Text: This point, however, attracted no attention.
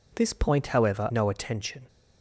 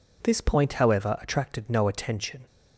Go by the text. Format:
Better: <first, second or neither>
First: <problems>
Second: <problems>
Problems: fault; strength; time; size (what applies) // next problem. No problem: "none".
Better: second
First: skips "attracted"; at 1.1 s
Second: none